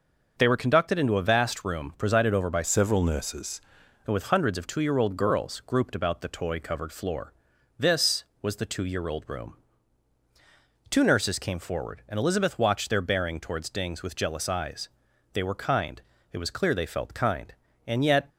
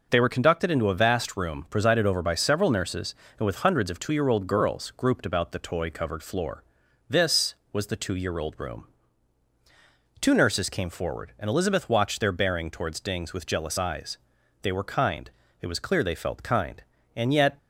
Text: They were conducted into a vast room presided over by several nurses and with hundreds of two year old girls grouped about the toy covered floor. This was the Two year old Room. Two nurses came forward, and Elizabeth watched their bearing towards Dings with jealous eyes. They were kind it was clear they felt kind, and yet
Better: second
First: starts louder than the rest; noticeable; until 1.3 s; 6 dB // changes voice from "several" to "nurses"; from 2.6 to 3.5 s; 0.9 s long // pauses between "kind" and "it"; slight; at 16.0 s; 0.32 s long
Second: pauses between "kind" and "it"; slight; at 15.2 s; 0.32 s long

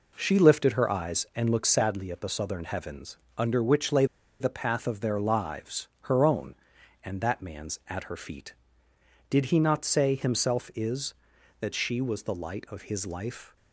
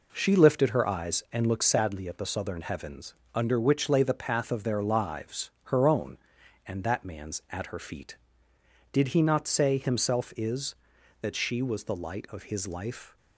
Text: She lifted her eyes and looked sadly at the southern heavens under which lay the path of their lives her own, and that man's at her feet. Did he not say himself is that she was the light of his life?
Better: second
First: pauses between "heavens" and "under"; slight; at 3.1 s; 0.20 s long // pauses between "lay" and "the"; slight; at 4.0 s; 0.35 s long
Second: pauses between "heavens" and "under"; slight; at 3.1 s; 0.20 s long

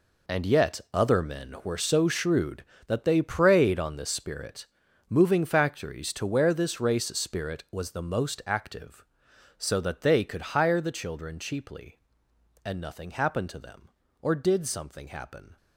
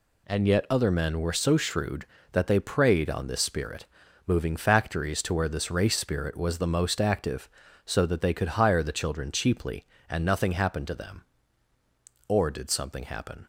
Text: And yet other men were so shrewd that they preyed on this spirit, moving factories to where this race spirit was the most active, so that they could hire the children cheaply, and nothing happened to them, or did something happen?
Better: second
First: gets quieter; strong; throughout; 13 dB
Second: none

